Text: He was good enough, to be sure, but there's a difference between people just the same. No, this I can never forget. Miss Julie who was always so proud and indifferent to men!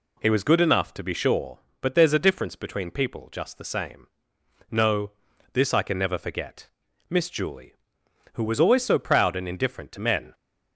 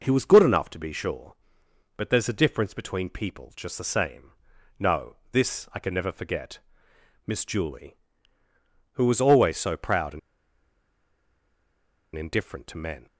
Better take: first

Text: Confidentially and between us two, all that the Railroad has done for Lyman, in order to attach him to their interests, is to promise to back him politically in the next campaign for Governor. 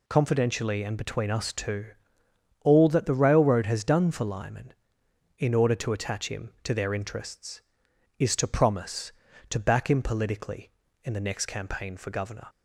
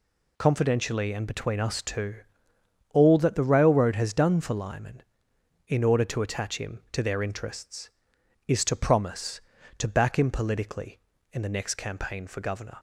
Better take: neither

